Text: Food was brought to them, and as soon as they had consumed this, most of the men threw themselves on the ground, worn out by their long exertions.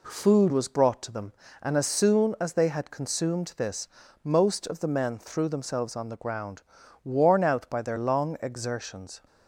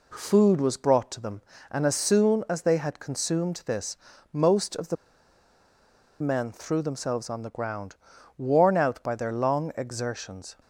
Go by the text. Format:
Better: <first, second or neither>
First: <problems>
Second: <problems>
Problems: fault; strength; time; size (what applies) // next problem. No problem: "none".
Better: first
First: none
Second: pauses between "the" and "men"; strong; at 4.9 s; 1.2 s long